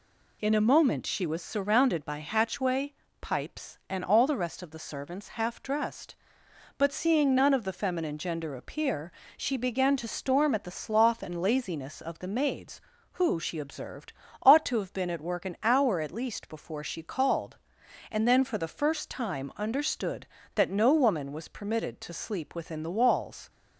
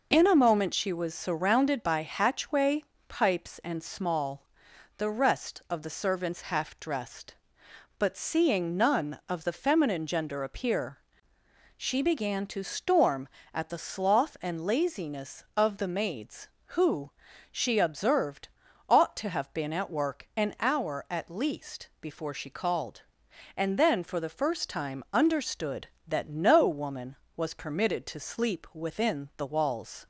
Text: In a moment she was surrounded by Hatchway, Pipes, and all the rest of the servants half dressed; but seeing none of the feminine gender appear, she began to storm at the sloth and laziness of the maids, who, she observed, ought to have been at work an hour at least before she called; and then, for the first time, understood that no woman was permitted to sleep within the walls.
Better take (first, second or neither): first